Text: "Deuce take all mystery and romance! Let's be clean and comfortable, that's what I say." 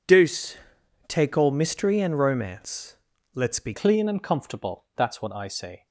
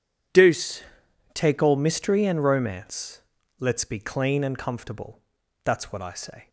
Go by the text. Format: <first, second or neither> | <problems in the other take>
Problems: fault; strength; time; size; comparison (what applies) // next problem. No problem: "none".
second | pauses between "Deuce" and "take"; noticeable; at 0.5 s; 0.52 s long; noticeable in the second // changes voice at "clean"; from 3.7 s on; 2.1 s long